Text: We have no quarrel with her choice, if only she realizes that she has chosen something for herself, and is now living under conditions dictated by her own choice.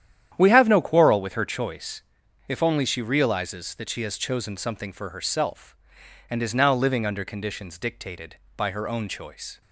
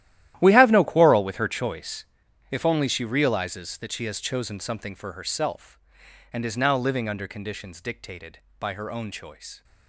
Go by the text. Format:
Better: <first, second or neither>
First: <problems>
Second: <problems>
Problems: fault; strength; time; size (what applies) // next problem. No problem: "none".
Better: first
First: starts louder than the rest; strong; until 1.3 s; 10 dB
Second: gets quieter; strong; throughout; 16.5 dB // starts louder than the rest; strong; until 1.4 s; 13 dB